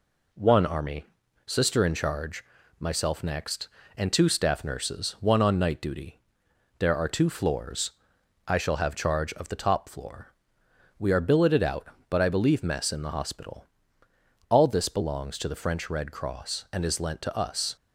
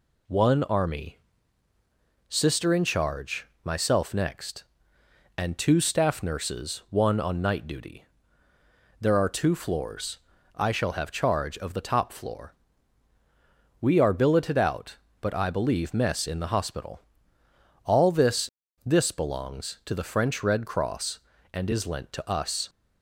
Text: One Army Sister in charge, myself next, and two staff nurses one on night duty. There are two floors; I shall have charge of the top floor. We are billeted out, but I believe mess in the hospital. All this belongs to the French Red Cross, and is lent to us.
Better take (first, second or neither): first